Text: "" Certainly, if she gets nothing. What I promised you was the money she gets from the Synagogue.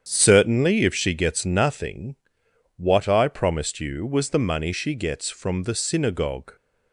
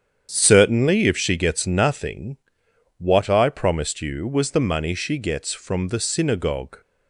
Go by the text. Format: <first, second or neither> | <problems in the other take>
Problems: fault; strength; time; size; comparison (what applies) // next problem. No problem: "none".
neither | starts louder than the rest; strong; the same in both